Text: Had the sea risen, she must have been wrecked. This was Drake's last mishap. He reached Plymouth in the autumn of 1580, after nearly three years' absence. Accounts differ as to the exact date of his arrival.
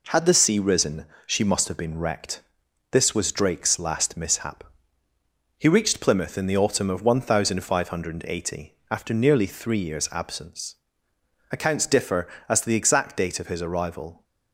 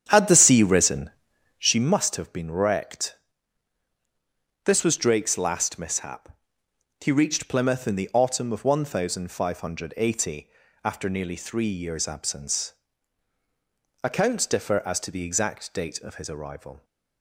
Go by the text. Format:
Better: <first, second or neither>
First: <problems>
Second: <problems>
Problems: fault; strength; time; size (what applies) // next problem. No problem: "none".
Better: first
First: none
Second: starts louder than the rest; strong; until 1.7 s; 9 dB